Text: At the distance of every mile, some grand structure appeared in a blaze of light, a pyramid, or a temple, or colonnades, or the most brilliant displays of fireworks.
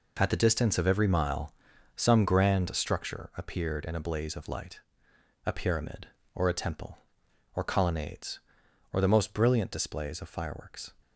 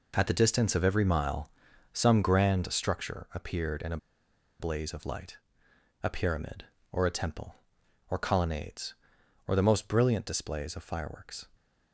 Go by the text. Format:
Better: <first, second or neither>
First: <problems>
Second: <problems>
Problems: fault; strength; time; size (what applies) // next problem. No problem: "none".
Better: first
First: none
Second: pauses between "a" and "blaze"; noticeable; at 3.9 s; 0.63 s long